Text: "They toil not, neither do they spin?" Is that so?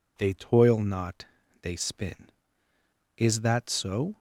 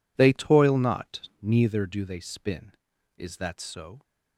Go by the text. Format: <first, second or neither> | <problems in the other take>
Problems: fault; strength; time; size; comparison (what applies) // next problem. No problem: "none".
second | skips "neither do"; at 1.4 s